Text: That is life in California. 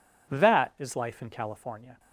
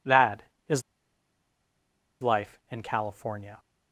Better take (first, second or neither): first